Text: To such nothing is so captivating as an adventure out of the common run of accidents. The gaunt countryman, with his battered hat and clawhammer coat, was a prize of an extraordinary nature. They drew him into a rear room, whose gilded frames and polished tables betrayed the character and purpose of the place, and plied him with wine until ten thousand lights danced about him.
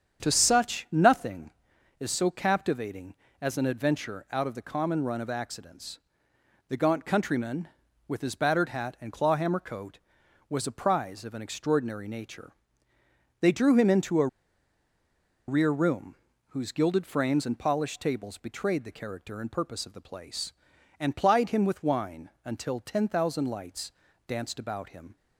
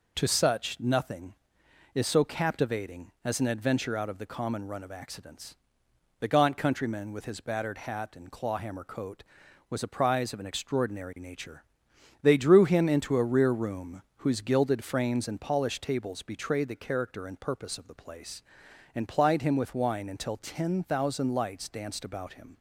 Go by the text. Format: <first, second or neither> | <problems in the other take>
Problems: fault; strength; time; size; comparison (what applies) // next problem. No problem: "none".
second | starts louder than the rest; strong; until 1.2 s; 8 dB // pauses between "a" and "rear"; at 14.2 s; 1.2 s long // pauses between "wine" and "until"; slight; at 22.2 s; 0.16 s long // pauses between "lights" and "danced"; slight; at 23.9 s; 0.34 s long